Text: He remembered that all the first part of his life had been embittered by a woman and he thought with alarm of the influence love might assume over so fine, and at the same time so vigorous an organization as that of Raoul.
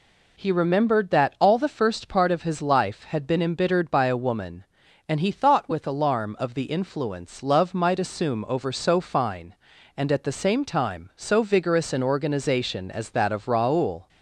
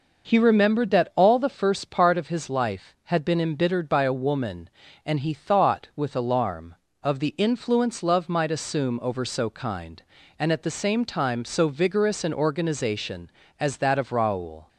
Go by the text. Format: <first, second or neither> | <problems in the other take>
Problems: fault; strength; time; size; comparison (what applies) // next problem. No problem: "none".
first | says "kind" for "fine"; at 9.4 s